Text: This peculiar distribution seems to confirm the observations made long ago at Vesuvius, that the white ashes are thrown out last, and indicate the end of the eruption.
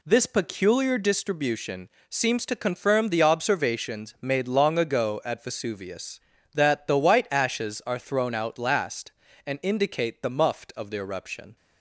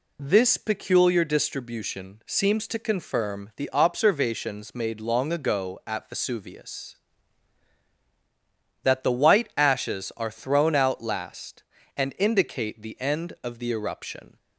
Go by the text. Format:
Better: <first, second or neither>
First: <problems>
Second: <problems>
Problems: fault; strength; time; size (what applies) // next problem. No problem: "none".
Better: second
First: pauses between "distribution" and "seems"; slight; at 1.8 s; 0.22 s long // says "muft" for "end"; at 10.2 s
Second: none